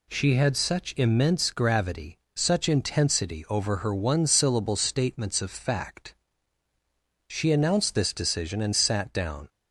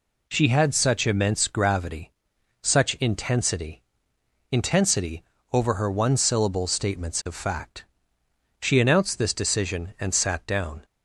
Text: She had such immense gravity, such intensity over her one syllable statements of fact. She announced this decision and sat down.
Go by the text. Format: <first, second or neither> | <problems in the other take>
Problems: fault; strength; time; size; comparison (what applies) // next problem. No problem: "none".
first | says "intensity" twice; at 4.4 s